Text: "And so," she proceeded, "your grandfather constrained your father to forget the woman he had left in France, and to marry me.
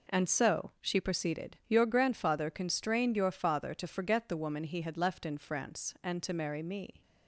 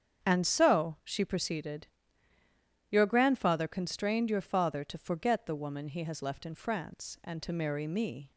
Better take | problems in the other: first | starts louder than the rest; strong; until 1.2 s; 8 dB // says "has" for "had"; at 6.0 s

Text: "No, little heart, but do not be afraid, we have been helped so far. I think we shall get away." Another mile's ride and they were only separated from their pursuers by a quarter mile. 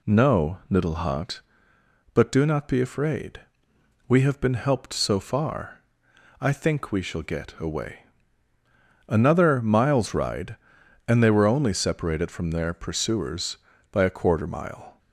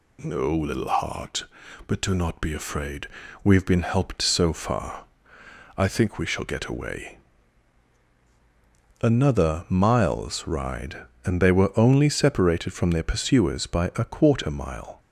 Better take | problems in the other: neither | none

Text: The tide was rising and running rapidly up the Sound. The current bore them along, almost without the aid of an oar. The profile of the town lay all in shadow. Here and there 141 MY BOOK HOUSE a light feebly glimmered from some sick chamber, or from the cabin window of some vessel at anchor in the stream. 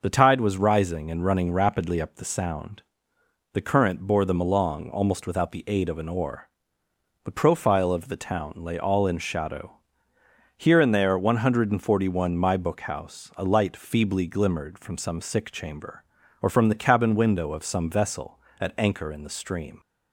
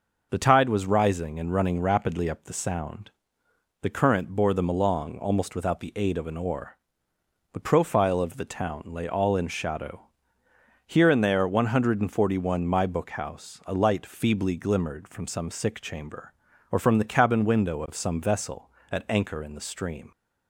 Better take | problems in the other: neither | none

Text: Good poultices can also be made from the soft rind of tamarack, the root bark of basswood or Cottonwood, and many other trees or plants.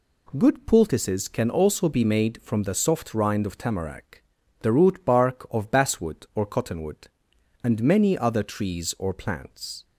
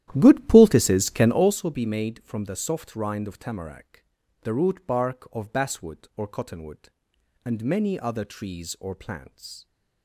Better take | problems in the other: first | starts louder than the rest; strong; until 1.6 s; 12.5 dB

